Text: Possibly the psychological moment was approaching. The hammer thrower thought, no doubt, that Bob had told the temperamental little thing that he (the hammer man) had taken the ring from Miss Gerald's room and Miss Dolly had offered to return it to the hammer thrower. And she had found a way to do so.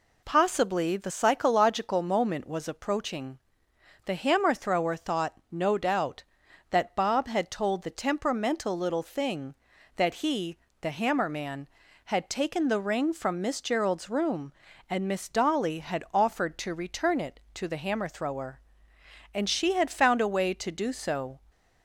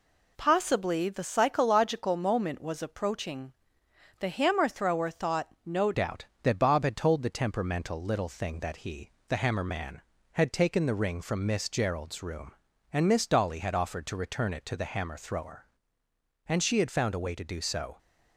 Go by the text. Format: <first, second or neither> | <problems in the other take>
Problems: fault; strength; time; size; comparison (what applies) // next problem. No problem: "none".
first | changes voice at "doubt"; from 5.9 s on; 12.0 s long